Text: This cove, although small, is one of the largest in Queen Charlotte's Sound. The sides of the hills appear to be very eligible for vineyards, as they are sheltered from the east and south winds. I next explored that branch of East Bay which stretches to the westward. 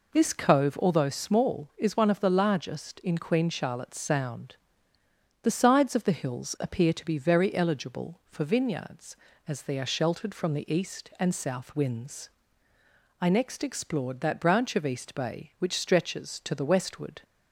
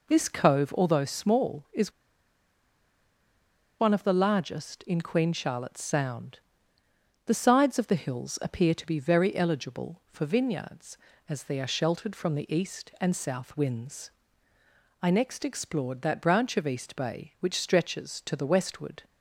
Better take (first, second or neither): first